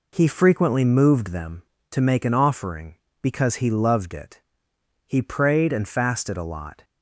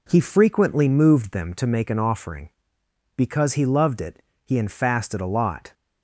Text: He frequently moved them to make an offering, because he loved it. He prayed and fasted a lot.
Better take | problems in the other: first | skips "prayed"; at 4.5 s

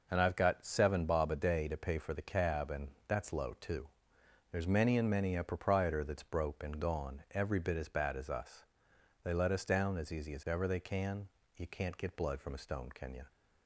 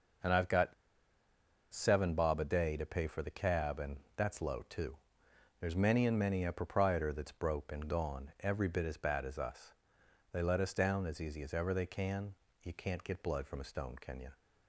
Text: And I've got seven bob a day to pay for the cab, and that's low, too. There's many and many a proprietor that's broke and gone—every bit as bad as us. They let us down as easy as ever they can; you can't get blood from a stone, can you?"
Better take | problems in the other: first | pauses between "got" and "seven"; at 0.7 s; 0.98 s long // pauses between "and" and "that's"; slight; at 3.9 s; 0.20 s long; slight in the first

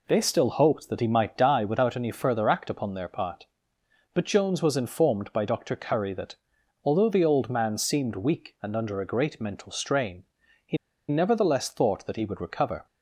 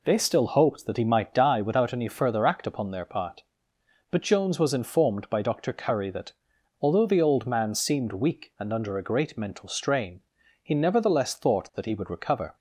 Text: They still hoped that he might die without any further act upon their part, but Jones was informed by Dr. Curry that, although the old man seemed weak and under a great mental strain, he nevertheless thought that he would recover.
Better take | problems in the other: second | pauses between "he" and "nevertheless"; slight; at 10.7 s; 0.32 s long

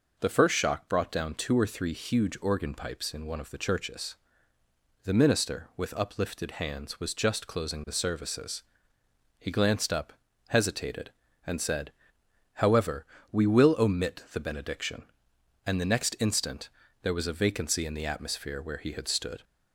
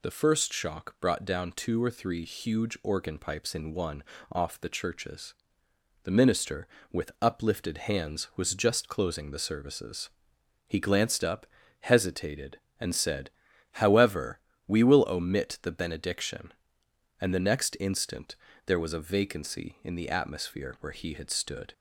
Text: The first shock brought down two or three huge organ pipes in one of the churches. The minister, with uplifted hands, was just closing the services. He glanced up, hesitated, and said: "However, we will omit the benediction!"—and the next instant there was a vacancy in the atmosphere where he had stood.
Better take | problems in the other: first | says "off" for "of"; at 4.3 s // pauses between "instant" and "there"; slight; at 18.3 s; 0.30 s long; slight in the first

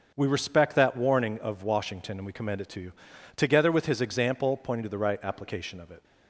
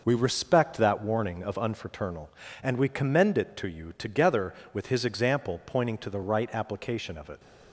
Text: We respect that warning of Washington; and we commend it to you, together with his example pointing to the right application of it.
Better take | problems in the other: first | says "Unfraternal" for "Washington"; at 1.5 s

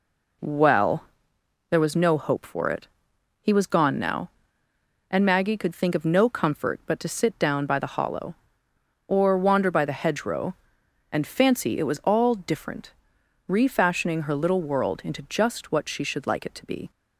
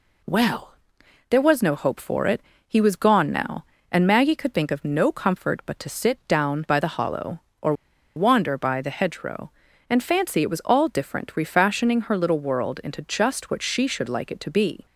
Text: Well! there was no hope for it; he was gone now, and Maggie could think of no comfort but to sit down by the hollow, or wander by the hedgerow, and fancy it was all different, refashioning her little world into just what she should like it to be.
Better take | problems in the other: first | pauses between "or" and "wander"; at 7.7 s; 0.43 s long

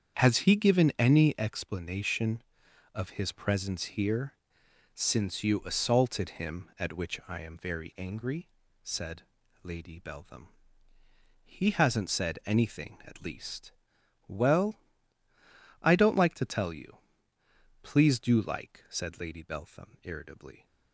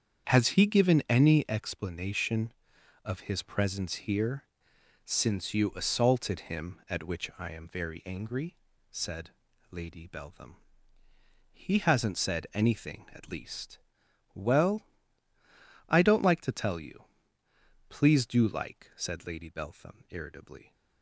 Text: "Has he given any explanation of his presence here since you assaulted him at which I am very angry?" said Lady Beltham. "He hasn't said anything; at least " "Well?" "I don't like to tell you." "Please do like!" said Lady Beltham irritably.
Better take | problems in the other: neither | starts louder than the rest; strong; the same in both // pauses between "here" and "since"; noticeable; the same in both // pauses between "said" and "Lady"; the same in both

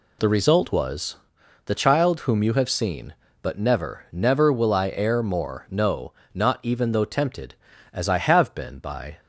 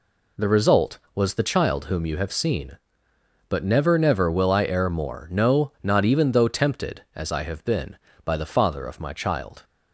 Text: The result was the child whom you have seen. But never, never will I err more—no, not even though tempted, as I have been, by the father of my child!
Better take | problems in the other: second | pauses between "was" and "the"; noticeable; at 1.1 s; 0.48 s long // stops before "the father of my child"; at 9.1 s

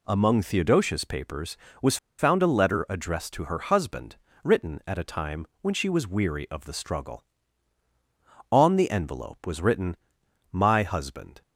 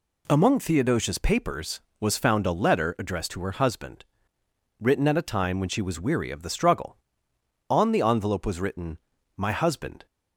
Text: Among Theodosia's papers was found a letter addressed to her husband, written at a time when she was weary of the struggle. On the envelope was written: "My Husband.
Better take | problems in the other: second | pauses between "was" and "found"; slight; at 1.9 s; 0.22 s long

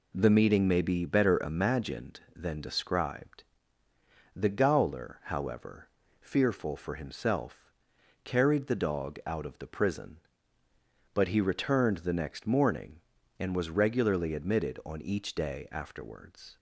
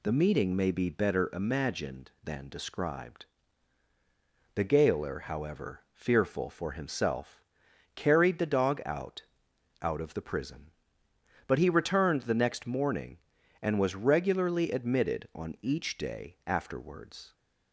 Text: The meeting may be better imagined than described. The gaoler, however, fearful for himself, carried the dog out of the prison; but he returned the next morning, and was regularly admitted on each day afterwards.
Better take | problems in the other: first | says "out" twice; at 9.8 s

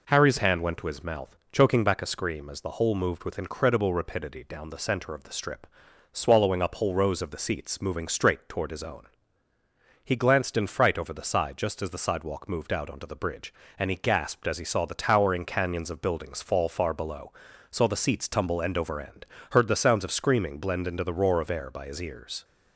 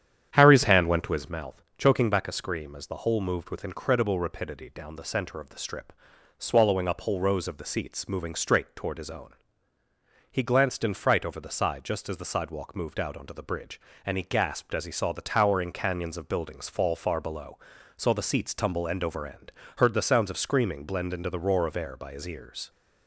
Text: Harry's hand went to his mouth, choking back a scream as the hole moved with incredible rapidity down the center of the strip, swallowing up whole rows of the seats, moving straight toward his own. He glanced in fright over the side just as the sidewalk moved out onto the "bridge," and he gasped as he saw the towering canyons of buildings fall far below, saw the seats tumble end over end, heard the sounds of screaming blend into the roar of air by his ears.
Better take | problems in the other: first | starts louder than the rest; strong; until 1.4 s; 9 dB

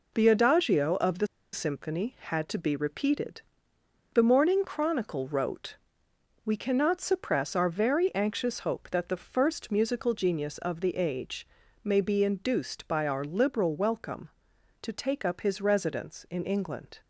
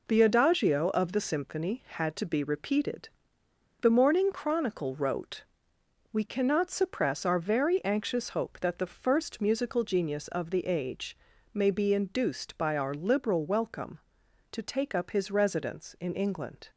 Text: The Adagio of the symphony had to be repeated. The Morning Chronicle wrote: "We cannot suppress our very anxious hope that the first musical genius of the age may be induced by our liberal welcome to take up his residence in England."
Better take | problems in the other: second | pauses between "the" and "symphony"; slight; at 1.2 s; 0.26 s long // pauses between "age" and "may"; at 11.4 s; 0.38 s long; also in the second

